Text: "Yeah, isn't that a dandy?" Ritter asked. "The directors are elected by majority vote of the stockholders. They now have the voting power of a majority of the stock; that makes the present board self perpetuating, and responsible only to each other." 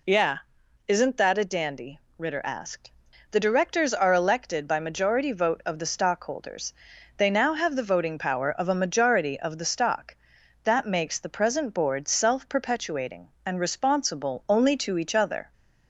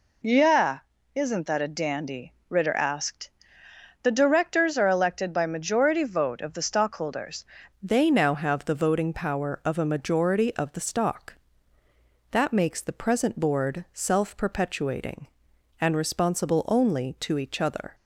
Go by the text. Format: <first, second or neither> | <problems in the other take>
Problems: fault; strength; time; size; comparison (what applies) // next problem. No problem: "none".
first | changes voice at "They"; from 7.8 s on; 10.1 s long